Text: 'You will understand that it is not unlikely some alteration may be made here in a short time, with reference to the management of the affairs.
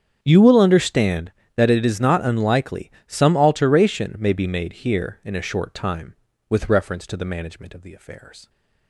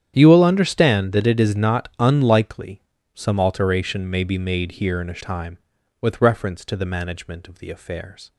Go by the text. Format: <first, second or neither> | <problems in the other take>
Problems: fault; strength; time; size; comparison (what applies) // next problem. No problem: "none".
first | starts louder than the rest; strong; until 1.1 s; 9.5 dB; strong in the first // pauses between "unlikely" and "some"; slight; at 2.8 s; 0.34 s long; slight in the first // skips "short"; at 5.2 s